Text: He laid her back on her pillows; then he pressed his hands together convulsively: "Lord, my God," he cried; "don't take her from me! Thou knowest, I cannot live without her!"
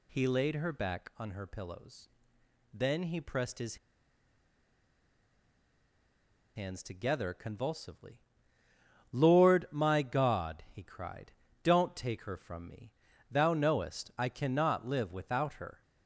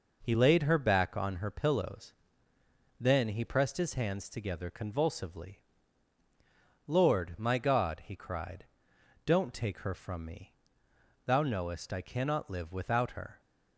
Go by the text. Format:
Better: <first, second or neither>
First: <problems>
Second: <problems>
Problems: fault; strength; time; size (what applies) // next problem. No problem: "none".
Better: second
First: pauses between "his" and "hands"; strong; at 3.7 s; 2.7 s long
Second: none